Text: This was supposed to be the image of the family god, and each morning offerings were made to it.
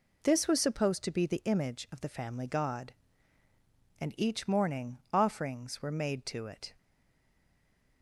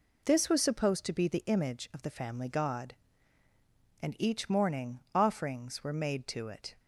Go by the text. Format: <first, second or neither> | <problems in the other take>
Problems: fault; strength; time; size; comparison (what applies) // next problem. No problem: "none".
second | stays silent after the last word; noticeable; from 6.7 s on; 1.3 s long